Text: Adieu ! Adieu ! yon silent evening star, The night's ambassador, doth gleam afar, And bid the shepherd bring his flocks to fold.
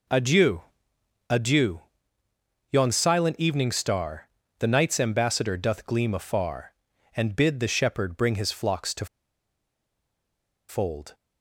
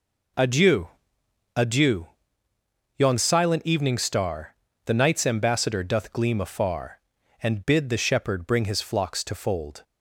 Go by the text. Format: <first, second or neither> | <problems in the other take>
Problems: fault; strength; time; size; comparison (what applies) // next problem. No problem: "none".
second | pauses between "to" and "fold"; strong; at 9.0 s; 1.6 s long